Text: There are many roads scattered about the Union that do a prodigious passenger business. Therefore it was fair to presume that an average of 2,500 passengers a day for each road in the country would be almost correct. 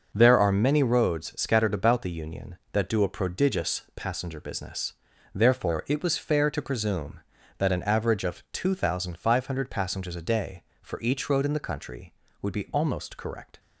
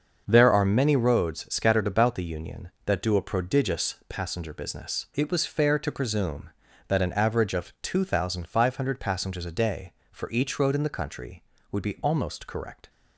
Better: first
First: none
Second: starts louder than the rest; until 1.2 s; 6.5 dB // skips "Therefore"; at 5.0 s

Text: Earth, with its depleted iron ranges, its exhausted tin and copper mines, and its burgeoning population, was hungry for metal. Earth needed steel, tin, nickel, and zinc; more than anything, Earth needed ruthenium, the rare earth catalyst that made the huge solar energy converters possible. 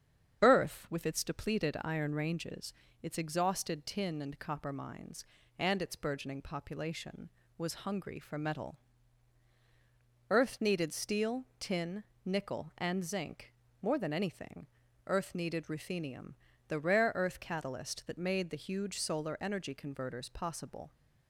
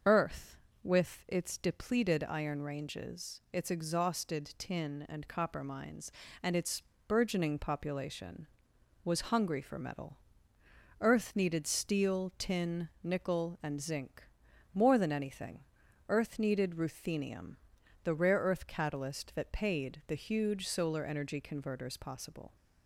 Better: first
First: starts louder than the rest; strong; until 1.4 s; 8 dB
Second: starts louder than the rest; until 1.3 s; 6.5 dB // pauses between "its" and "burgeoning"; slight; at 6.8 s; 0.24 s long // says "paid" for "made"; at 19.5 s

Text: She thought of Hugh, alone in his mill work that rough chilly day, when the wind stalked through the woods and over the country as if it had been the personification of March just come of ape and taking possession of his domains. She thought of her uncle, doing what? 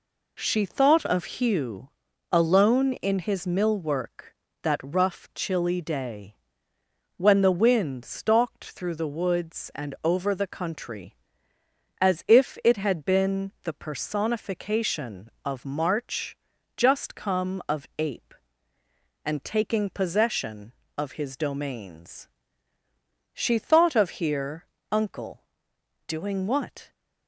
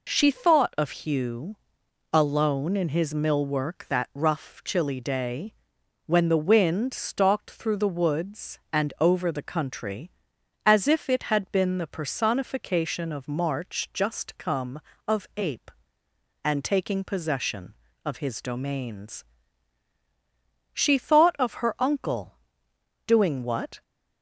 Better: second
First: pauses between "March" and "just"; at 16.3 s; 0.40 s long // says "here" for "her"; at 24.2 s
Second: none

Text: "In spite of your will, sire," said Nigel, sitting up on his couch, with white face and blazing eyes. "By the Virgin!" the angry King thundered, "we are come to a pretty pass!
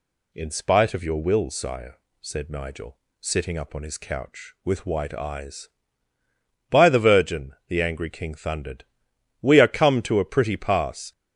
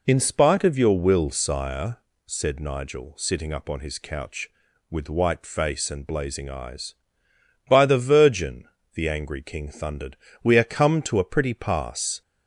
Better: second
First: skips "face and blazing"; at 5.1 s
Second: none

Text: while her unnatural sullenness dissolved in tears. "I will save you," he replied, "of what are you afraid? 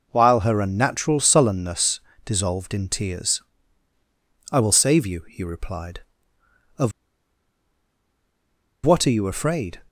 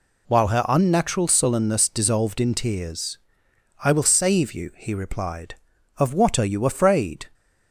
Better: second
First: pauses between "sullenness" and "dissolved"; slight; at 2.0 s; 0.24 s long // pauses between "of" and "what"; strong; at 6.9 s; 1.9 s long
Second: none

